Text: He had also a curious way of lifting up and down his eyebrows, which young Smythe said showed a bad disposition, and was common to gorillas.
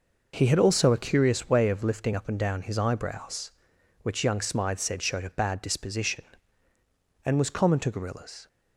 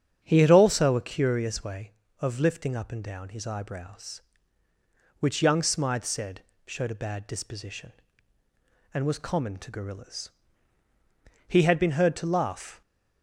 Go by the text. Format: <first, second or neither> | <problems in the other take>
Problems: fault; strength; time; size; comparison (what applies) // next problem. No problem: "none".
first | starts louder than the rest; strong; until 1.2 s; 8.5 dB // pauses between "said" and "showed"; slight; at 6.4 s; 0.26 s long // goes on to say "He had been heard to laugh"; from 11.4 s on; 1.3 s long